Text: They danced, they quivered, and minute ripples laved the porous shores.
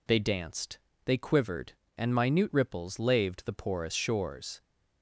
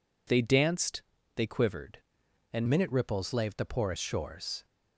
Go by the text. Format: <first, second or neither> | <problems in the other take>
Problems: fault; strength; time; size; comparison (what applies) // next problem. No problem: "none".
first | changes voice at "minute"; from 2.6 s on; 2.0 s long